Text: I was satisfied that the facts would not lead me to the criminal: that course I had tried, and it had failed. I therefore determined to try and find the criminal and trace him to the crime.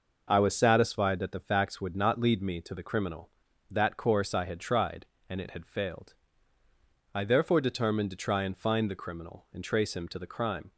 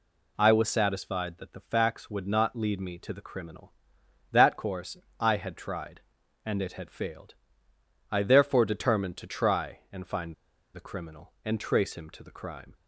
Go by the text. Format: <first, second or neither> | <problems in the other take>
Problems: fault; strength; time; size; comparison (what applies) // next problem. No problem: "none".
first | pauses between "course" and "I"; slight; at 4.9 s; 0.22 s long // pauses between "find" and "the"; at 10.3 s; 0.41 s long